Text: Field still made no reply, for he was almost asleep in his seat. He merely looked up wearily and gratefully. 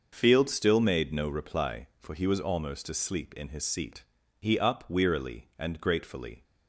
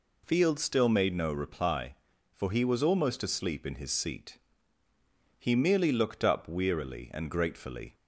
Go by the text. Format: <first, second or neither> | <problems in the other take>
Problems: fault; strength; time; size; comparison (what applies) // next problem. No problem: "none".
second | starts louder than the rest; until 1.1 s; 6 dB // skips "merely looked"; at 4.5 s